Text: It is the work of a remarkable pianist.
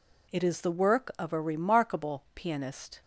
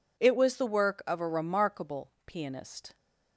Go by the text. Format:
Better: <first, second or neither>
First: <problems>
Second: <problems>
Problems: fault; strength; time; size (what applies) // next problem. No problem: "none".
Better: first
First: none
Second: says "was" for "is"; at 0.3 s // pauses between "remarkable" and "pianist"; slight; at 2.0 s; 0.16 s long